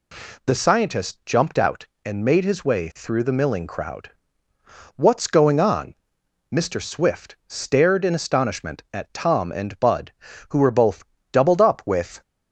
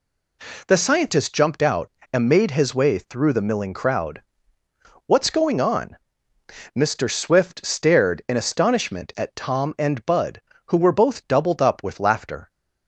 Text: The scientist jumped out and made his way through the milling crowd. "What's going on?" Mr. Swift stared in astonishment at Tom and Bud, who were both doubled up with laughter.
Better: second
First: pauses between "both" and "doubled"; slight; at 11.0 s; 0.30 s long // stops before "laughter"; at 12.2 s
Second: none

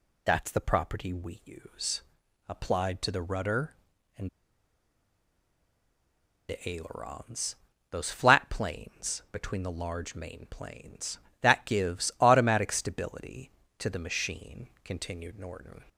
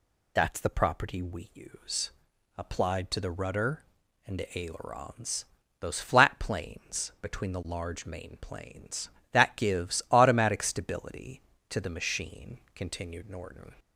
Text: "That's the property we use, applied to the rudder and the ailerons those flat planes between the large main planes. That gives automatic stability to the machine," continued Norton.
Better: second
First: pauses between "and" and "the"; strong; at 4.2 s; 2.1 s long // pauses between "ailerons" and "those"; slight; at 7.5 s; 0.36 s long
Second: pauses between "ailerons" and "those"; slight; at 5.4 s; 0.36 s long

